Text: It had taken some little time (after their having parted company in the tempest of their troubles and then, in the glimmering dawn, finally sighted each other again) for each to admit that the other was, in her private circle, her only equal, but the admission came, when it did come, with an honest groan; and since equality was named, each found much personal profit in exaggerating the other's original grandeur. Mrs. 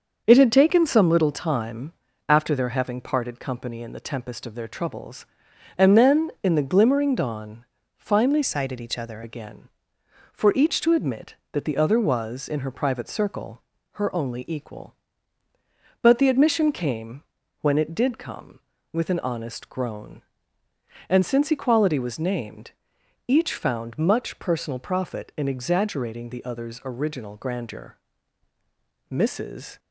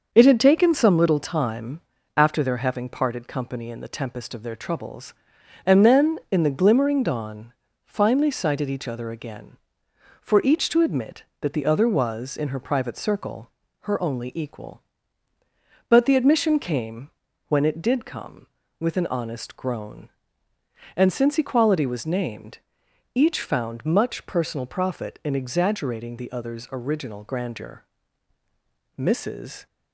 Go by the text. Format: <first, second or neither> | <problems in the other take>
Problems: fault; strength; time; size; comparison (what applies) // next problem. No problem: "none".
second | starts louder than the rest; until 1.2 s; 6.5 dB; also in the second // changes voice from "sighted" to "other"; from 8.4 to 9.2 s; 0.8 s long